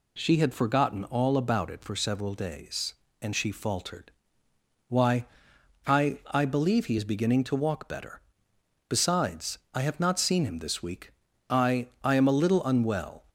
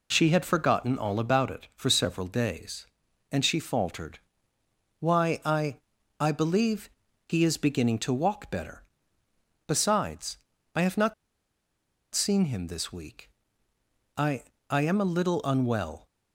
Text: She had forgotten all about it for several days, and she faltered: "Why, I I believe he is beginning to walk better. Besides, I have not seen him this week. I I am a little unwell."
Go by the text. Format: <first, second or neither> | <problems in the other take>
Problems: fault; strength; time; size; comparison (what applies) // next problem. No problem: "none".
first | pauses between "I" and "I"; at 5.7 s; 0.42 s long // pauses between "believe" and "he"; at 6.8 s; 0.40 s long // pauses between "not" and "seen"; at 11.1 s; 0.99 s long // pauses between "I" and "I"; slight; at 14.4 s; 0.26 s long